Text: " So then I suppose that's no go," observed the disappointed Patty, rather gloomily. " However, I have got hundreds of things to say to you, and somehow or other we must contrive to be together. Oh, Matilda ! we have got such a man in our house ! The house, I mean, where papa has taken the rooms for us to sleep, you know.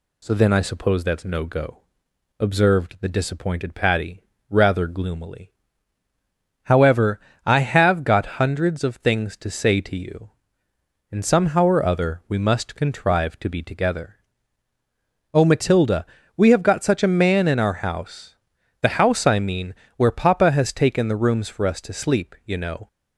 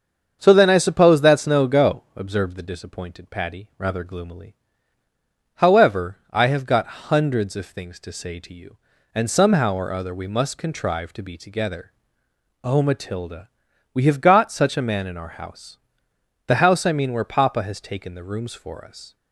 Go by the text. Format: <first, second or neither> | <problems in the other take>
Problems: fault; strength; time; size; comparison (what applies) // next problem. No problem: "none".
first | starts louder than the rest; strong; until 1.4 s; 7.5 dB // stops before "to sleep you know"; at 19.1 s